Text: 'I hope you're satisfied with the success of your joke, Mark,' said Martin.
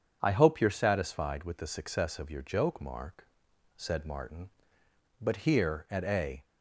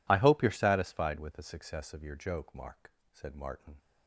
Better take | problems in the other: second | starts louder than the rest; strong; until 1.2 s; 7.5 dB // goes on to say "But here at a"; noticeable; from 5.1 s on; 1.2 s long

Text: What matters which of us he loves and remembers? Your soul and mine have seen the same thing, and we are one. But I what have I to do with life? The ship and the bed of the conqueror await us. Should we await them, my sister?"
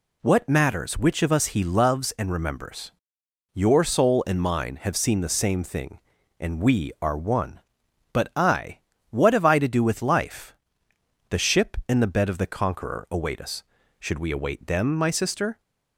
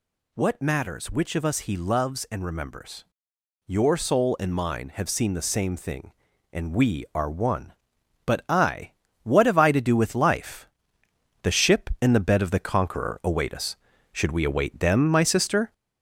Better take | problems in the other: first | gets louder; slight; throughout; 3 dB // pauses between "I" and "what"; slight; at 8.9 s; 0.32 s long; slight in the first

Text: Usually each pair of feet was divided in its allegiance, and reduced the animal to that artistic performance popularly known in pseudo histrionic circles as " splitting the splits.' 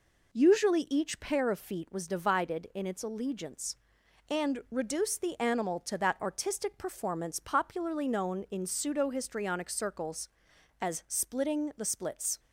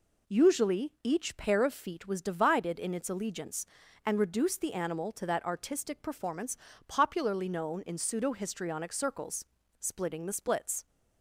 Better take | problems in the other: first | pauses between "performance" and "popularly"; slight; at 6.5 s; 0.32 s long // skips "as"; at 9.5 s

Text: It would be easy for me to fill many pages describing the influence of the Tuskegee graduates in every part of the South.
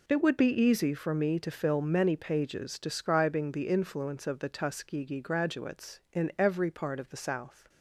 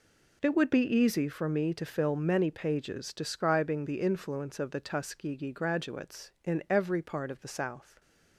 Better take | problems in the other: neither | none

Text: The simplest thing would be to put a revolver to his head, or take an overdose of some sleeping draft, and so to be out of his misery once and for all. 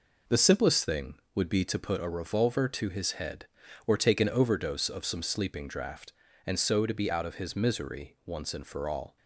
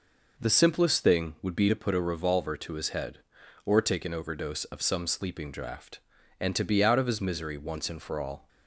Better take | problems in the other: first | skips "so"; at 6.5 s

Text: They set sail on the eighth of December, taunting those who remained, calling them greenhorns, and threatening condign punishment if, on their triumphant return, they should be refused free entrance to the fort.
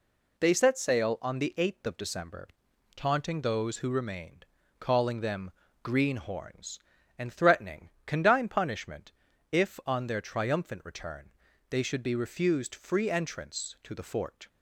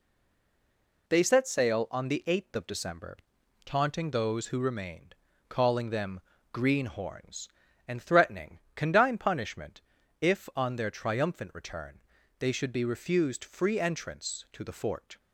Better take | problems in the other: first | stays silent before the first word; until 1.0 s; 1.0 s long // pauses between "them" and "greenhorns"; slight; at 6.2 s; 0.32 s long; slight in the first // pauses between "threatening" and "condign"; slight; at 8.5 s; 0.16 s long; slight in the first // pauses between "punishment" and "if"; at 9.8 s; 0.40 s long; also in the first

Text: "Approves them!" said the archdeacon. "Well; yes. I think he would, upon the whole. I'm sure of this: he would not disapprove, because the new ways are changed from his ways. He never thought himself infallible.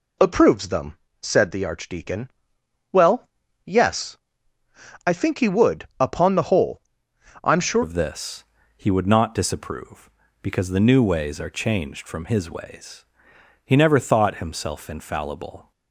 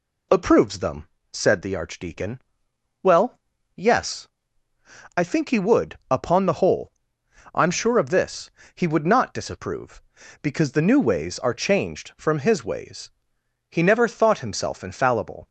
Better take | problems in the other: second | changes voice at "of"; from 7.8 s on; 7.9 s long

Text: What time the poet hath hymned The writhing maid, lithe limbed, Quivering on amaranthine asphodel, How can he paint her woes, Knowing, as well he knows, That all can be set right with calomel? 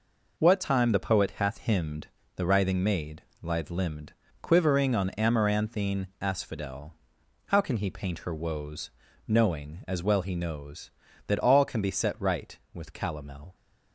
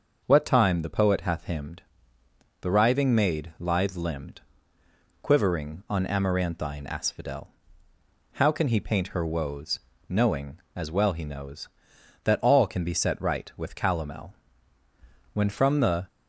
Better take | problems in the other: first | starts louder than the rest; noticeable; until 1.2 s; 6 dB // pauses between "hymned" and "The"; noticeable; at 1.8 s; 0.80 s long; slight in the first // goes on to say "When from the"; noticeable; from 15.3 s on; 0.74 s long

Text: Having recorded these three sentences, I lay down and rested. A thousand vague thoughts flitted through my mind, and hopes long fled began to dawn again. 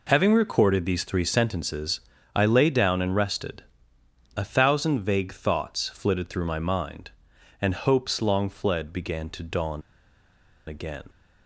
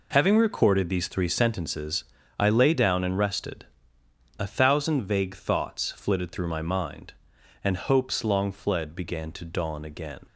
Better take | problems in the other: second | pauses between "dawn" and "again"; noticeable; at 9.8 s; 0.87 s long

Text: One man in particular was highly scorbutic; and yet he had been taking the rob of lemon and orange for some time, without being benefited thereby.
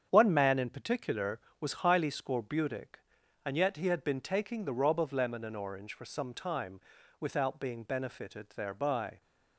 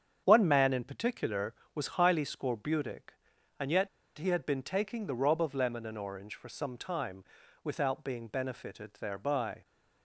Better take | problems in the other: first | starts louder than the rest; strong; until 1.2 s; 8 dB; strong in the first // pauses between "yet" and "he"; slight; at 3.8 s; 0.29 s long

